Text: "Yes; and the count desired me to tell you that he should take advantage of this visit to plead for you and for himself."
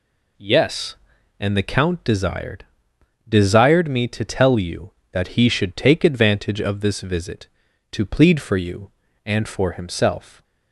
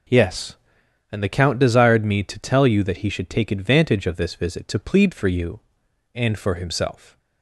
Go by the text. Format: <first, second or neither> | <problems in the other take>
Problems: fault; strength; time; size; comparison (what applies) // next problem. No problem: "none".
second | says "desired" twice; at 3.2 s